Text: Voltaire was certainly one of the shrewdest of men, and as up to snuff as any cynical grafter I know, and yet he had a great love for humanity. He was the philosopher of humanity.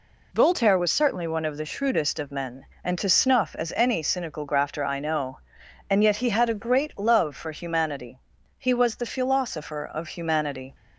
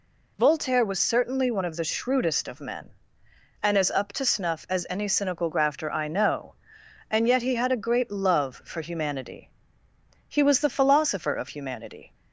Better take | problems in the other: second | skips "as up"; at 2.9 s

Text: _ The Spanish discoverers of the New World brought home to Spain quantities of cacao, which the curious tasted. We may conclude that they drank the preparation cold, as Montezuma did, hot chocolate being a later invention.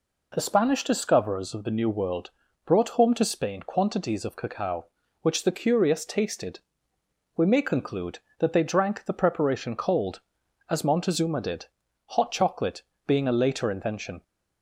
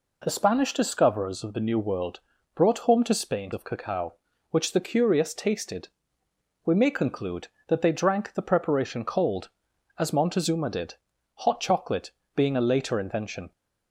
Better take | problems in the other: first | pauses between "World" and "brought"; slight; at 2.2 s; 0.34 s long; slight in the first // skips "quantities"; at 3.5 s // pauses between "chocolate" and "being"; slight; at 12.0 s; 0.24 s long; slight in the first

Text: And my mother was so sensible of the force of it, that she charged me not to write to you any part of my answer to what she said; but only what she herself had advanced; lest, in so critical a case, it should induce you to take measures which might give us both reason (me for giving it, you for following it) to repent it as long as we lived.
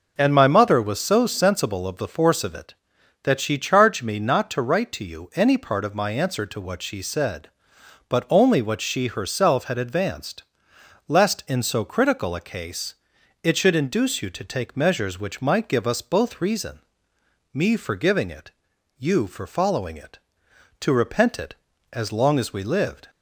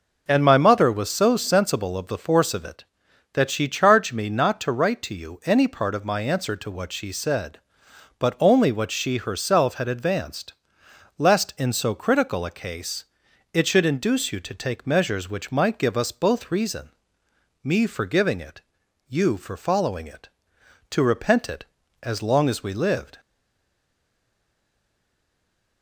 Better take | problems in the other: first | stays silent after the last word; strong; from 23.1 s on; 2.7 s long

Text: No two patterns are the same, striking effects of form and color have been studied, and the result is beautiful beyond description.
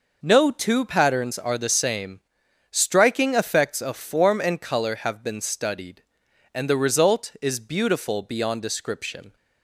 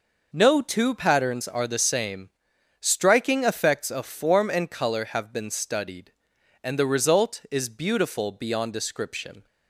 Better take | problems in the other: neither | none

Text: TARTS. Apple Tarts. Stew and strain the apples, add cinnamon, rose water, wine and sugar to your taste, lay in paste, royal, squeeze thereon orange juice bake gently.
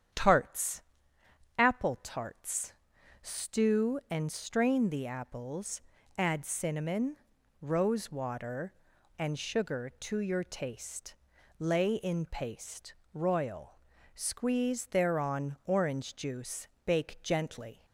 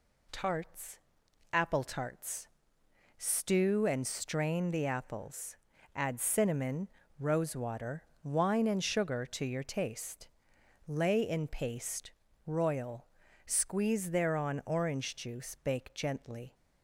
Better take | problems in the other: second | starts louder than the rest; strong; until 1.8 s; 9 dB // skips "wine"; at 8.9 s // pauses between "juice" and "bake"; slight; at 16.6 s; 0.18 s long

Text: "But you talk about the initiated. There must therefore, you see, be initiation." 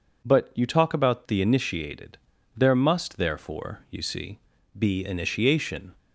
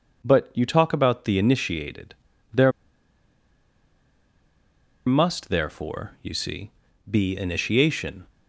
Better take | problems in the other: first | pauses between "There" and "must"; strong; at 2.7 s; 2.3 s long

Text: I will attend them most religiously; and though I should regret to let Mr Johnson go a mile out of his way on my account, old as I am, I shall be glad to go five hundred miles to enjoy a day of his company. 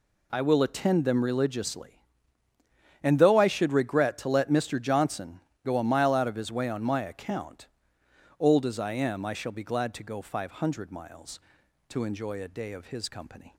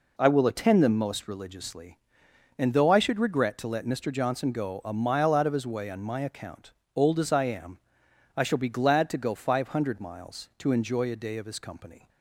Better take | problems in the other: second | skips "most"; at 1.2 s // pauses between "Johnson" and "go"; slight; at 5.4 s; 0.24 s long

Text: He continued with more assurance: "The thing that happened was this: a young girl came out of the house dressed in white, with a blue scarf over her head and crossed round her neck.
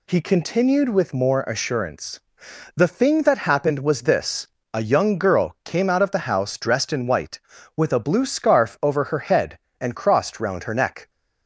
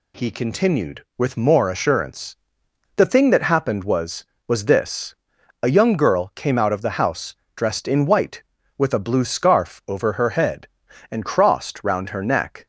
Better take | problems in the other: first | says "was" twice; at 4.4 s // pauses between "house" and "dressed"; slight; at 7.3 s; 0.22 s long

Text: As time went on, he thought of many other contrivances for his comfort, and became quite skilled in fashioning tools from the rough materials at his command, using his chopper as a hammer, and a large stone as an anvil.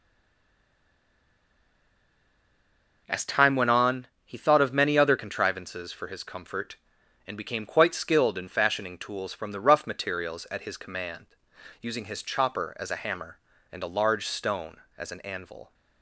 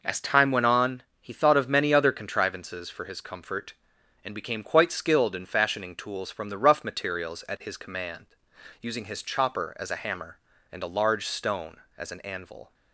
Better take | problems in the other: second | stays silent before the first word; strong; until 3.0 s; 3.0 s long

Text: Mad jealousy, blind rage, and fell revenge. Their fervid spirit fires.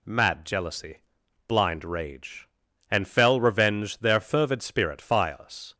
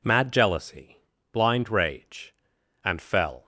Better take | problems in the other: first | stops before "revenge Their fervid spirit fires"; at 3.4 s

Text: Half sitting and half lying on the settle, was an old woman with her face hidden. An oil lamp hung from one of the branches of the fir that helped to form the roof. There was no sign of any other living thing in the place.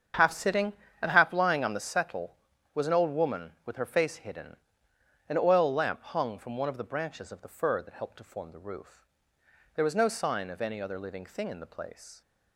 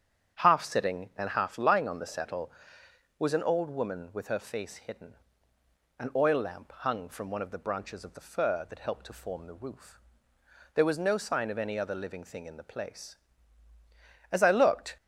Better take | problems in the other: first | starts louder than the rest; strong; until 1.4 s; 8 dB; strong in the first // goes on to say "As I looked"; noticeable; from 14.3 s on; 0.66 s long

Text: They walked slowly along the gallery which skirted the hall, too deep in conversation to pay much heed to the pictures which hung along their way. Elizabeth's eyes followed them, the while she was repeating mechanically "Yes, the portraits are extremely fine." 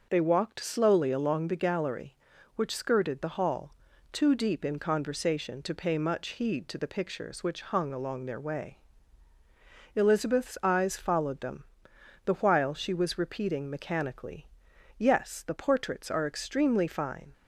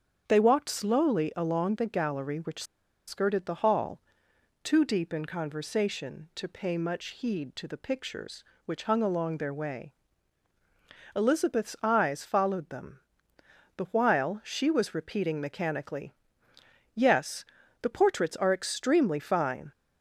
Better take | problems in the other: first | starts louder than the rest; strong; until 1.2 s; 7.5 dB // pauses between "which" and "skirted"; at 2.6 s; 0.44 s long // pauses between "mechanically" and "Yes"; noticeable; at 16.1 s; 0.84 s long; noticeable in the first

